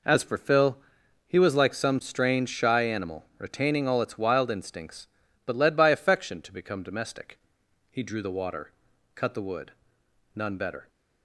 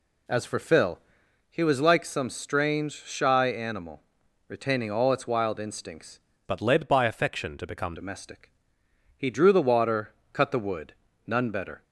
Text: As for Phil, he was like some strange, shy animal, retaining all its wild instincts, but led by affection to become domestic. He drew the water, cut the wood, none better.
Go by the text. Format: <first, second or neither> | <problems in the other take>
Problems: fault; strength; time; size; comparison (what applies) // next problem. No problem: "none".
first | changes voice from "but" to "become"; from 6.4 to 7.9 s; 1.5 s long